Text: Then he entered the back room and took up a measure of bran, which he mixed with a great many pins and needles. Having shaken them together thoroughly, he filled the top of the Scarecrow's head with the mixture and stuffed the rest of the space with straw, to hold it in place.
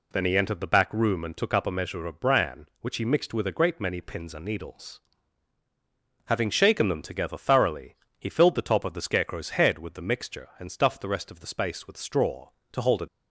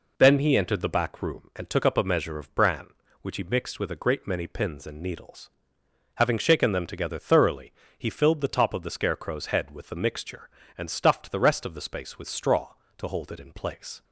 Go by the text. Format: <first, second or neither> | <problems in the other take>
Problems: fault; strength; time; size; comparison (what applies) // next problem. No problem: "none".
second | stops before "in place"; at 13.0 s